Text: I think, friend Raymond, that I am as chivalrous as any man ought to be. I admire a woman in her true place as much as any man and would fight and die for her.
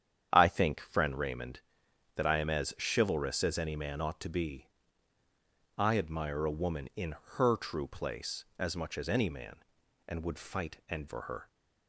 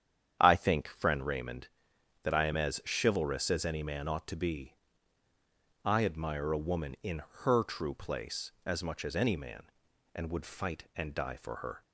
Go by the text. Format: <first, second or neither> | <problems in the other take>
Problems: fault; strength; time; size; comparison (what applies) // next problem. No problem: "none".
second | starts louder than the rest; strong; until 1.3 s; 8.5 dB; strong in the second // pauses between "in" and "her"; slight; at 7.1 s; 0.18 s long; slight in the second // skips "die"; at 11.0 s